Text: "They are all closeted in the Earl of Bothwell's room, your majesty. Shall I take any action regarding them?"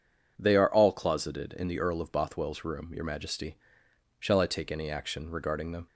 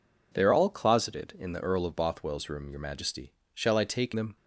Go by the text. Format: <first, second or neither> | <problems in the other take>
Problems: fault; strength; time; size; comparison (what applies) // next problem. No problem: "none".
first | skips "any action regarding"; at 4.1 s